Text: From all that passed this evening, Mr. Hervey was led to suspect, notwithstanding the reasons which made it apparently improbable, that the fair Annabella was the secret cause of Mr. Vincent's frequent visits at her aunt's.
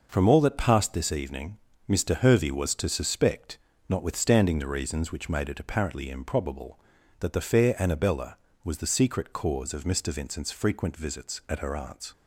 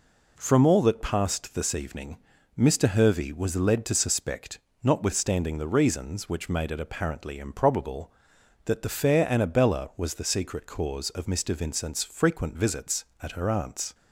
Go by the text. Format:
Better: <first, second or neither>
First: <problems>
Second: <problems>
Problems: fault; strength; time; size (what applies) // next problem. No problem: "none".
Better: second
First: skips "led"; at 2.7 s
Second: none